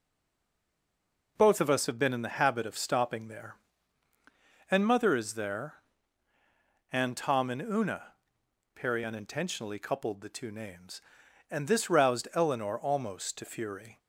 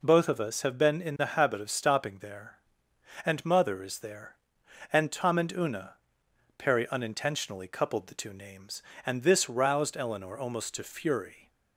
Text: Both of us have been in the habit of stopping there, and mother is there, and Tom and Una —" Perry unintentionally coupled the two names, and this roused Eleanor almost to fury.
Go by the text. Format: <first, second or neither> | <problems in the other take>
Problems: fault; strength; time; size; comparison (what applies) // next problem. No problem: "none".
second | stays silent before the first word; noticeable; until 1.3 s; 1.3 s long